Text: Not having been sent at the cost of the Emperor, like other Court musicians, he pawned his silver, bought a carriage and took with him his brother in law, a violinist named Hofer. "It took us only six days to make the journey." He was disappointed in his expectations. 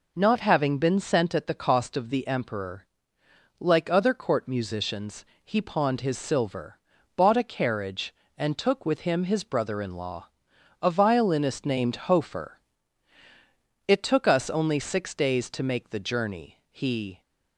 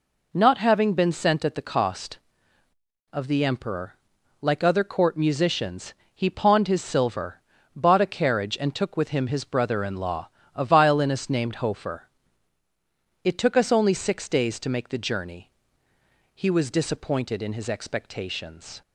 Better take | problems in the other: second | stops before "was disappointed in his expectations"; at 17.2 s

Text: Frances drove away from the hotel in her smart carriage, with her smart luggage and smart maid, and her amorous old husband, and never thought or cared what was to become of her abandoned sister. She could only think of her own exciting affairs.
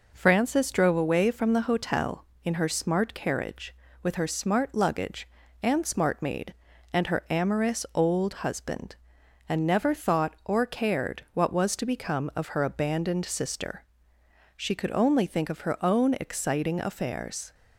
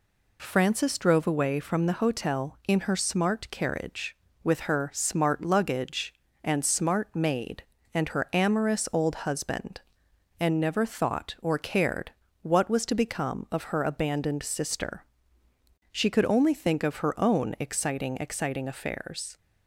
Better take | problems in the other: first | pauses between "cared" and "what"; slight; at 12.1 s; 0.30 s long // says "exciting" twice; at 18.1 s

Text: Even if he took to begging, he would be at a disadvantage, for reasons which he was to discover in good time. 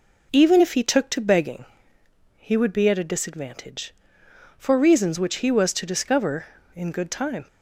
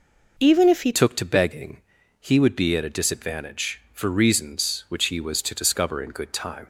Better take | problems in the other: first | changes voice at "took"; from 0.9 s on; 5.7 s long

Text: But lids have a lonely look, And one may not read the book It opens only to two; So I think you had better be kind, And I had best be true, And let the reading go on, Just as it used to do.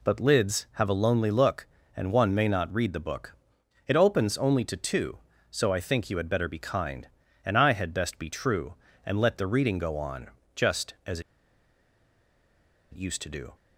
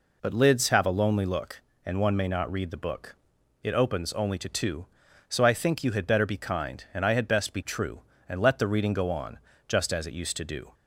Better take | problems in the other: second | pauses between "book" and "It"; noticeable; at 3.3 s; 0.52 s long; noticeable in the second // pauses between "as" and "it"; strong; at 11.1 s; 1.7 s long

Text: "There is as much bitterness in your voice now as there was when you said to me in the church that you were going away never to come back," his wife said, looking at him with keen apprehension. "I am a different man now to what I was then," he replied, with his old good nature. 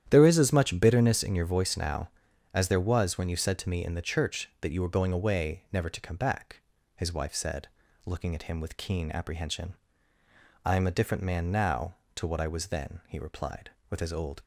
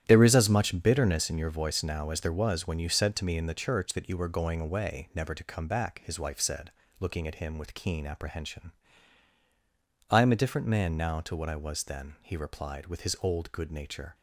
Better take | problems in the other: second | starts louder than the rest; strong; until 1.0 s; 10.5 dB; strong in the second // stops before "good nature"; at 14.4 s

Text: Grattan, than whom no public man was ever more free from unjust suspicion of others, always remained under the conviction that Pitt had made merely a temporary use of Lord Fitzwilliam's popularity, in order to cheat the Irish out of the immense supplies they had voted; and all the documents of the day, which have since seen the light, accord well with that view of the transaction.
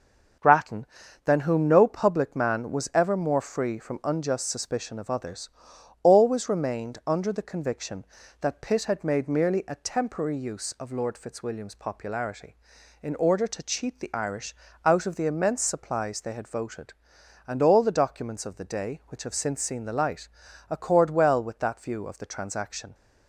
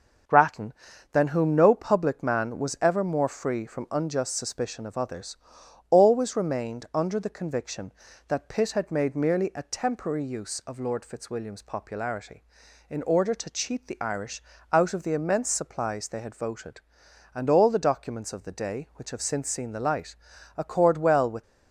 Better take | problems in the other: first | starts louder than the rest; until 1.6 s; 6.5 dB; also in the first // pauses between "Irish" and "out"; slight; at 14.4 s; 0.30 s long; slight in the first // stops before "that view of the transaction"; at 21.4 s

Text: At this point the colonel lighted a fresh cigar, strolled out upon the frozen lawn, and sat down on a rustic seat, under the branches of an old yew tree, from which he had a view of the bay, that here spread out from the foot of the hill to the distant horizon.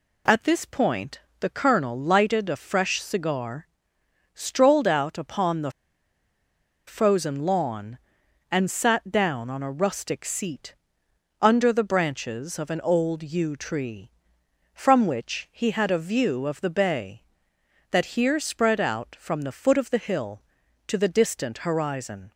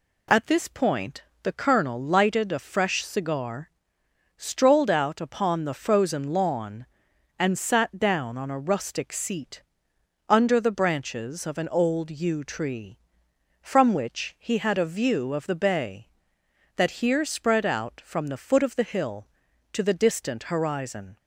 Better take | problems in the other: second | pauses between "point" and "the"; slight; at 1.2 s; 0.18 s long; slight in the second // pauses between "the" and "frozen"; at 5.7 s; 1.1 s long

